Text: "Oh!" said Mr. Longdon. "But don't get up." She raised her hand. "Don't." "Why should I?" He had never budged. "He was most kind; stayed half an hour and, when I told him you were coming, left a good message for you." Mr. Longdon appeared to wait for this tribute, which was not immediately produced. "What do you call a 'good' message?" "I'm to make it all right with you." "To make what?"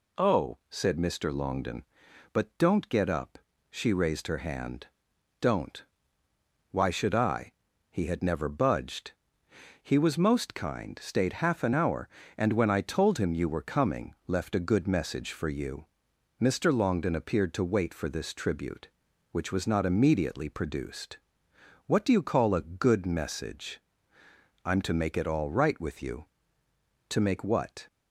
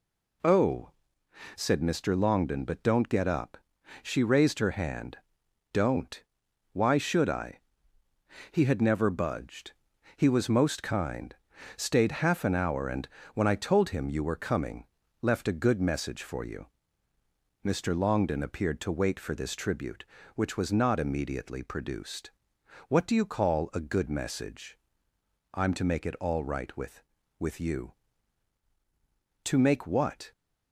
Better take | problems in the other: first | says "with" twice; at 27.3 s

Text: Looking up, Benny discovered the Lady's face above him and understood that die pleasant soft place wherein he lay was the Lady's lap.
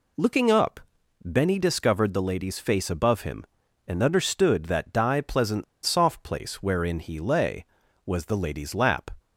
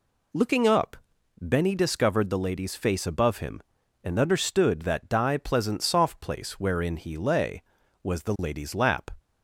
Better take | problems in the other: second | pauses between "pleasant" and "soft"; slight; at 5.6 s; 0.21 s long

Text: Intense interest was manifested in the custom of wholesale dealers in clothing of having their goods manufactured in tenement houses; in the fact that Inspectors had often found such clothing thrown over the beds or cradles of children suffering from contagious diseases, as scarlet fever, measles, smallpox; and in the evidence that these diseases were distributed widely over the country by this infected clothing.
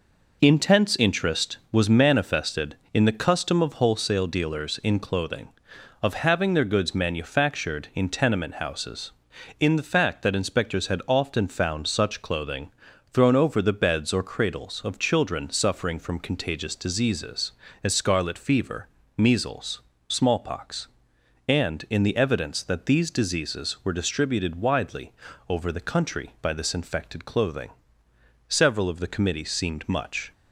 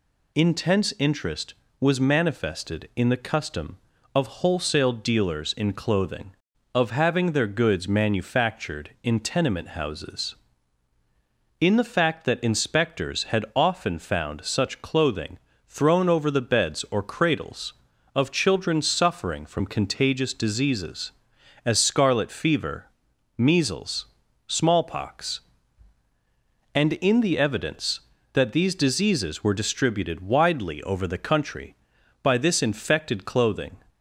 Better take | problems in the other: second | pauses between "clothing" and "thrown"; at 12.7 s; 0.40 s long; slight in the second // pauses between "widely" and "over"; at 25.1 s; 0.38 s long // goes on to say "Several of the committee seemed much"; strong; from 28.5 s on; 1.8 s long

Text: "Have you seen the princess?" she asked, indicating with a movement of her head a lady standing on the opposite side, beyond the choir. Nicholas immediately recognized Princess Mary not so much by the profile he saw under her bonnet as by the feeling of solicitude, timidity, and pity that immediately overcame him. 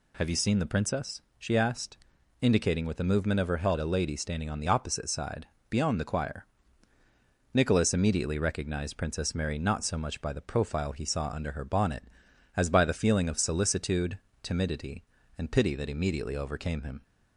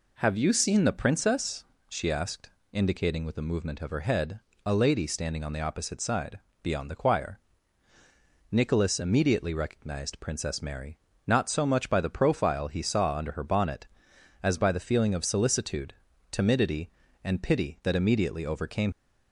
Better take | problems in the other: first | pauses between "head" and "a"; slight; at 4.3 s; 0.24 s long // pauses between "Mary" and "not"; slight; at 10.9 s; 0.28 s long // stops before "him"; at 18.9 s

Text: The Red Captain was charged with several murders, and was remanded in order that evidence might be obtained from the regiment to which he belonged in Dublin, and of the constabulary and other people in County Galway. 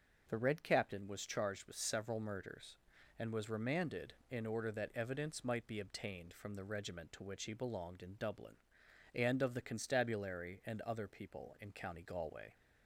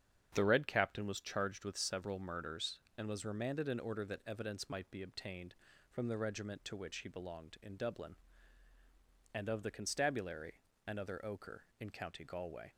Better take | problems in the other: first | starts louder than the rest; strong; until 1.3 s; 8 dB // says "ochre" for "people"; at 11.2 s

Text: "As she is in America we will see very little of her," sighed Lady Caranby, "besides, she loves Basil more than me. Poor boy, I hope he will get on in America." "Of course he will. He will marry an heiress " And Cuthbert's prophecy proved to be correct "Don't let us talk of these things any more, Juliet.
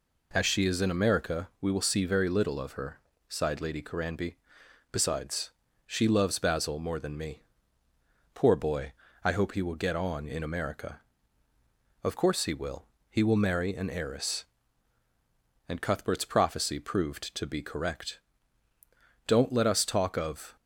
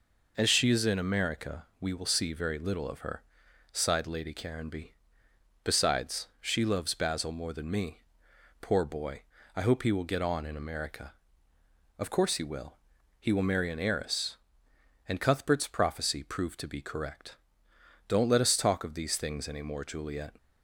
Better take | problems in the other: second | pauses between "correct" and "Don't"; at 18.1 s; 1.0 s long; noticeable in the second // stops before "these things any more Juliet"; at 20.5 s

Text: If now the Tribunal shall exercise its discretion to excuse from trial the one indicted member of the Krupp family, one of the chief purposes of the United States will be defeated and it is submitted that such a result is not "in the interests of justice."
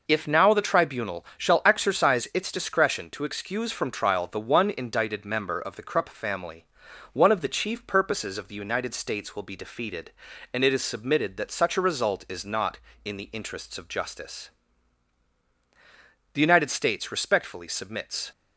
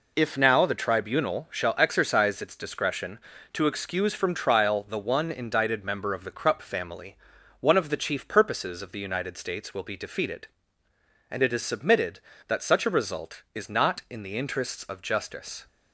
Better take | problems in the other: second | goes on to say "The United States respectfully submits"; strong; from 16.3 s on; 1.9 s long

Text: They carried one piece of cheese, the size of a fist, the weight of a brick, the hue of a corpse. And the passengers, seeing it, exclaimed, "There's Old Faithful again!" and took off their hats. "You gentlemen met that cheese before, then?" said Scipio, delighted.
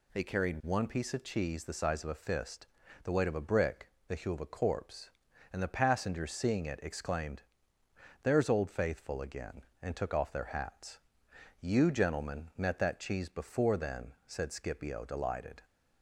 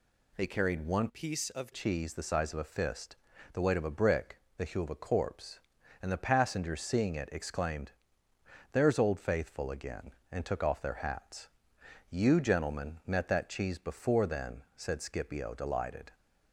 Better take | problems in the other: first | changes voice from "piece" to "of"; from 1.0 to 1.7 s; 0.7 s long

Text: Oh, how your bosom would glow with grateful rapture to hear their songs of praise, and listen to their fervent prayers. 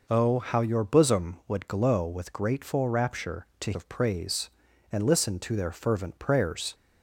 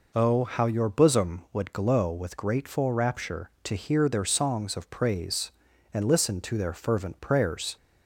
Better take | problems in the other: second | skips "hear their songs"; at 3.7 s

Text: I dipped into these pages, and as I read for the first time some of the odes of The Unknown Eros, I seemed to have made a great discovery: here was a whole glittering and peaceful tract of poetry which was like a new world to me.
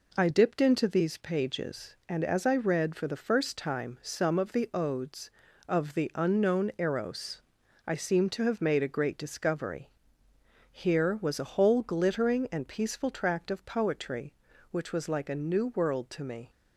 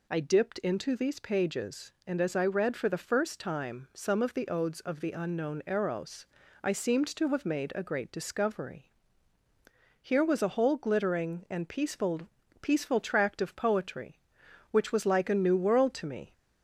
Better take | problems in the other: first | says "peaceful" twice; at 12.6 s

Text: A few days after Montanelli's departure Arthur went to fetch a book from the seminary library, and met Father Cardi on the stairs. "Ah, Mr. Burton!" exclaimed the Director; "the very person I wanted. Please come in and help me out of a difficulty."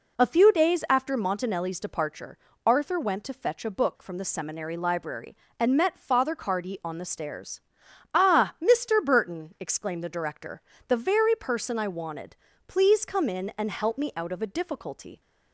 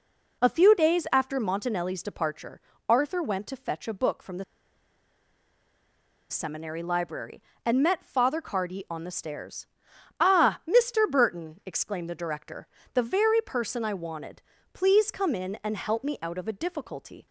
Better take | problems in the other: first | pauses between "departure" and "Arthur"; slight; at 2.6 s; 0.28 s long; slight in the first // pauses between "the" and "seminary"; strong; at 4.4 s; 1.8 s long

